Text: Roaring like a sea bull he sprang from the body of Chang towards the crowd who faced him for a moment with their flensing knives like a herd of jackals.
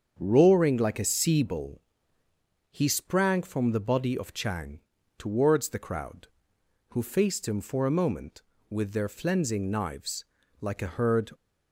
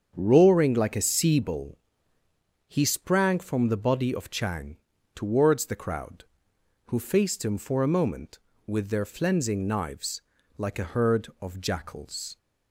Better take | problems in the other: second | starts louder than the rest; strong; until 1.1 s; 7 dB; strong in the second // pauses between "bull" and "he"; noticeable; at 1.8 s; 0.88 s long; noticeable in the second // pauses between "Chang" and "towards"; at 4.8 s; 0.38 s long; also in the second // pauses between "knives" and "like"; slight; at 10.2 s; 0.34 s long; slight in the second // stops before "of jackals"; at 11.3 s

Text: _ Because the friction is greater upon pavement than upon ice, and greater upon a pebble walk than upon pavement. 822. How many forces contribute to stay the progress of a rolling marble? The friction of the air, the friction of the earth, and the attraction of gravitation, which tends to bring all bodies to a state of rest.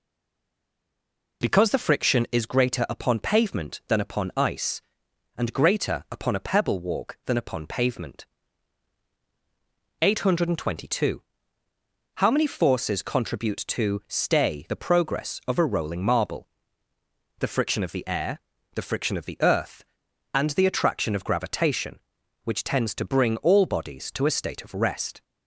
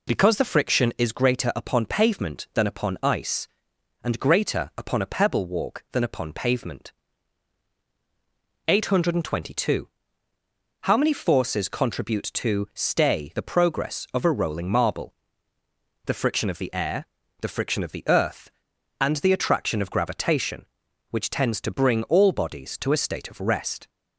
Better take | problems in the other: second | stays silent before the first word; noticeable; until 1.4 s; 1.4 s long

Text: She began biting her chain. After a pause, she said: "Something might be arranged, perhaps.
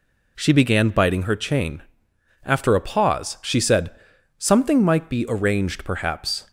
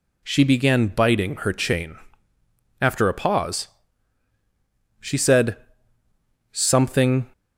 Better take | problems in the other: first | stops before "might be arranged perhaps"; at 7.3 s

